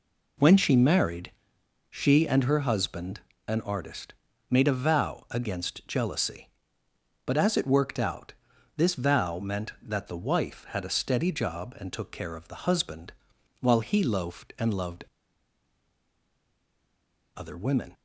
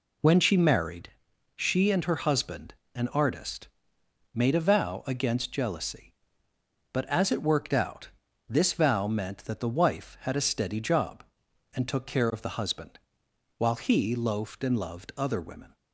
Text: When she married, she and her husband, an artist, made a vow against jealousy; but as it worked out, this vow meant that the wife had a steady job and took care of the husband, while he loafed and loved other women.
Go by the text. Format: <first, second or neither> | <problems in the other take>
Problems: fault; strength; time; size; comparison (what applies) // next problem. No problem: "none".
second | pauses between "loved" and "other"; strong; at 15.0 s; 2.3 s long